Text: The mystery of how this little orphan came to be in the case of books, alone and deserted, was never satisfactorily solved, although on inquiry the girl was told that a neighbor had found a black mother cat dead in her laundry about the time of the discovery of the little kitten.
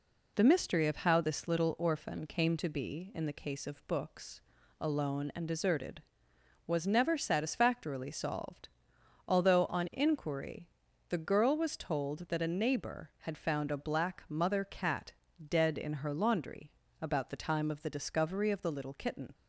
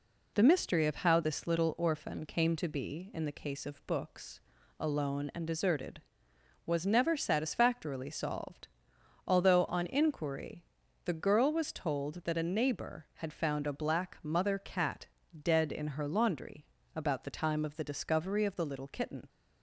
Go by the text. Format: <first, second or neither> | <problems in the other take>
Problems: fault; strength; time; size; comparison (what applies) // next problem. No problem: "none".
neither | pauses between "inquiry" and "the"; the same in both // pauses between "cat" and "dead"; slight; the same in both // pauses between "laundry" and "about"; slight; the same in both